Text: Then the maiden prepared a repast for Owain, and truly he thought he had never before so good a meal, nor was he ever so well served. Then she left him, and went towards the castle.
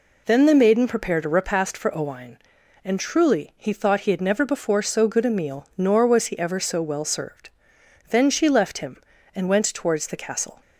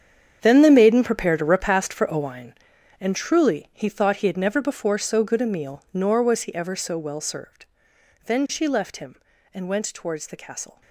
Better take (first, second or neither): first